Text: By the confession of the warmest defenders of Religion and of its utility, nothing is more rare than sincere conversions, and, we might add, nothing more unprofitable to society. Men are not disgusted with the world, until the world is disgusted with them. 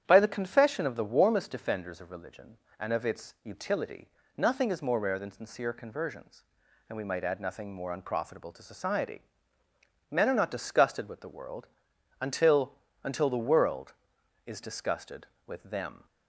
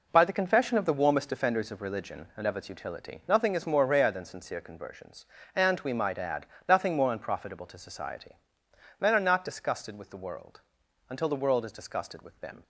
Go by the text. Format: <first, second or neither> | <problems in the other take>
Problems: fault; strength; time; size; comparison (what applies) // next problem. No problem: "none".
second | starts louder than the rest; strong; until 1.0 s; 9.5 dB // says "until" twice; at 13.0 s